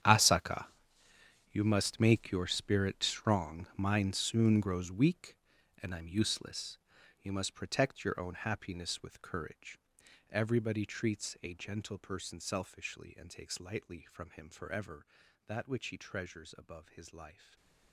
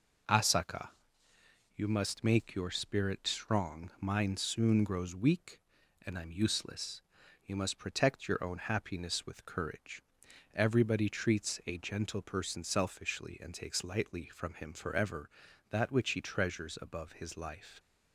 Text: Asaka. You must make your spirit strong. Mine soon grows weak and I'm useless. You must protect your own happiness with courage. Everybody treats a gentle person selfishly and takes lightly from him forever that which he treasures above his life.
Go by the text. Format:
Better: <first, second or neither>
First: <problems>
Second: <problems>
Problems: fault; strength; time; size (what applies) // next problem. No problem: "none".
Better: second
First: gets quieter; strong; throughout; 16 dB // stays silent after the last word; slight; from 17.3 s on; 0.6 s long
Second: none